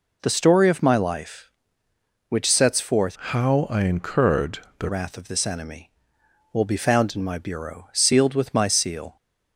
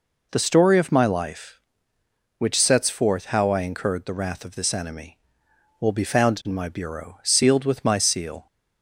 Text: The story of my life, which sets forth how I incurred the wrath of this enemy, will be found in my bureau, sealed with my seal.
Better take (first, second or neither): second